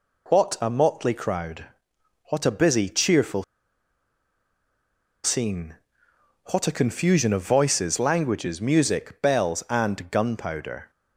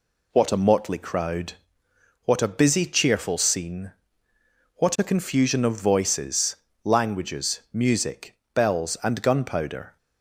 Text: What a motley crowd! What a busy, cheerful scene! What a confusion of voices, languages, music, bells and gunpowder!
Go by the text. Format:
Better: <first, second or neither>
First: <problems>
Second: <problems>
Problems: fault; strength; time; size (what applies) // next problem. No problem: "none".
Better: second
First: pauses between "cheerful" and "scene"; strong; at 3.4 s; 1.8 s long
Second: none